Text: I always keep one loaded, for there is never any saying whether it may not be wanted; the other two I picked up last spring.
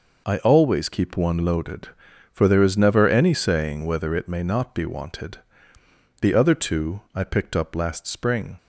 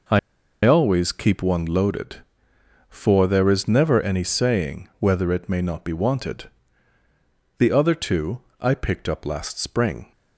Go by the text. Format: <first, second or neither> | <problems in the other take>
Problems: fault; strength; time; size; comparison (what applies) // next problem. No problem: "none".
first | pauses between "I" and "always"; noticeable; at 0.1 s; 0.46 s long // pauses between "two" and "I"; slight; at 8.3 s; 0.20 s long